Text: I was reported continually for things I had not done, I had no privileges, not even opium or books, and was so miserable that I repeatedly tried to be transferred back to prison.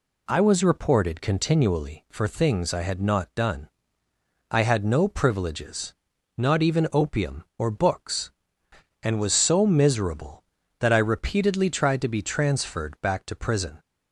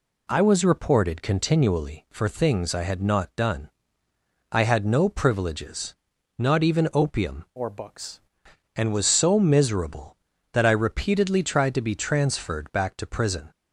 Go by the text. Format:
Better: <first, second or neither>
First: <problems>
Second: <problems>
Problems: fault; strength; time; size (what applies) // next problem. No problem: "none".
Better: first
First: none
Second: changes voice from "or" to "books"; from 7.5 to 8.1 s; 0.6 s long